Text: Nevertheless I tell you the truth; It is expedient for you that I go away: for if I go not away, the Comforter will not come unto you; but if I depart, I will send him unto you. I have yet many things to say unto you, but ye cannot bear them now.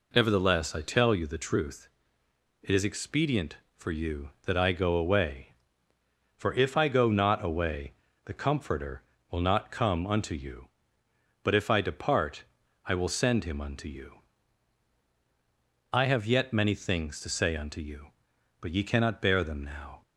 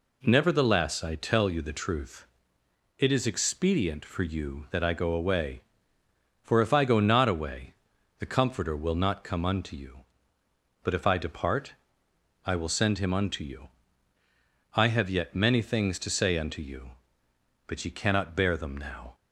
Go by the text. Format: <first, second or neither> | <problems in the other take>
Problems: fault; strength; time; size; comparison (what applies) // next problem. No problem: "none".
neither | none